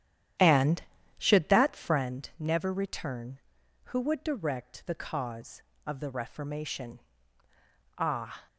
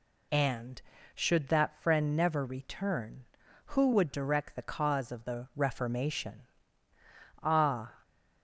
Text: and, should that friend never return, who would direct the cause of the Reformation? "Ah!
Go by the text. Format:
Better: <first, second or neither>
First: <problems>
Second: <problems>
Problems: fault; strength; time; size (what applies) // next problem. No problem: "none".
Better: second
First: starts louder than the rest; strong; until 2.1 s; 10.5 dB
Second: none